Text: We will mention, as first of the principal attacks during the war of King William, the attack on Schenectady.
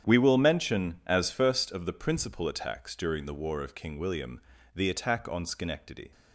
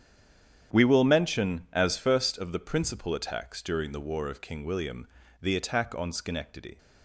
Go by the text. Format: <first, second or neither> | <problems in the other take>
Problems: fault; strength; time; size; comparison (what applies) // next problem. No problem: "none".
first | stays silent before the first word; slight; until 0.7 s; 0.7 s long // starts louder than the rest; strong; until 1.8 s; 9 dB; strong in the first